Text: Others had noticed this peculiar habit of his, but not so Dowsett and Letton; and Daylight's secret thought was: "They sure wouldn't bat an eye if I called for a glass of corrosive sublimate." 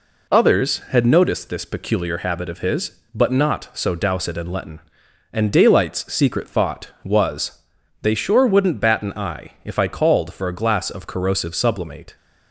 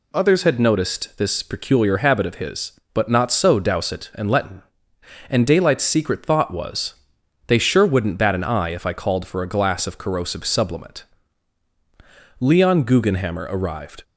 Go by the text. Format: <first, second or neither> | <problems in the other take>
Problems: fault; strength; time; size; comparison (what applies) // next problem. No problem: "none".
first | goes on to say "Leon Guggenhammer arrived"; from 12.4 s on; 1.6 s long